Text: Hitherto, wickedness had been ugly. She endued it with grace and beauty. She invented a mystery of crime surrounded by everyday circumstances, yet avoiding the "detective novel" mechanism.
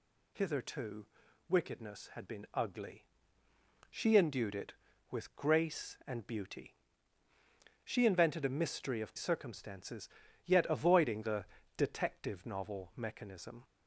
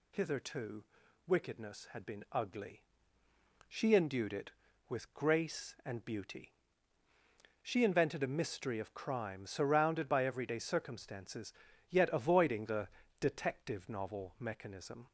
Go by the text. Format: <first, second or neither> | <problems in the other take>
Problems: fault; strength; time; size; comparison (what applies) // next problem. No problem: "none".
second | skips "crime surrounded by everyday"; at 9.1 s // pauses between "the" and "detective"; slight; at 11.4 s; 0.32 s long; slight in the second